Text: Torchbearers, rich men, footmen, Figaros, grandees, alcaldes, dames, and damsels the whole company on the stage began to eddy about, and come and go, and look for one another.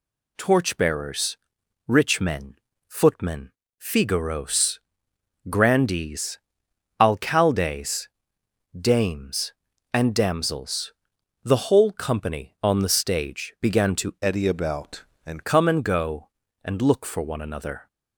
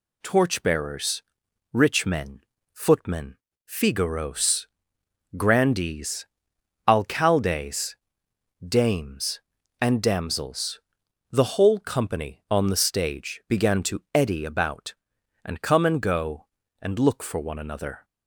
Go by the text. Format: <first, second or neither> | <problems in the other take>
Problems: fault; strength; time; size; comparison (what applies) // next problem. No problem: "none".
second | pauses between "damsels" and "the"; noticeable; at 10.9 s; 0.52 s long; noticeable in the second // changes voice from "eddy" to "and"; from 14.2 to 15.4 s; 1.2 s long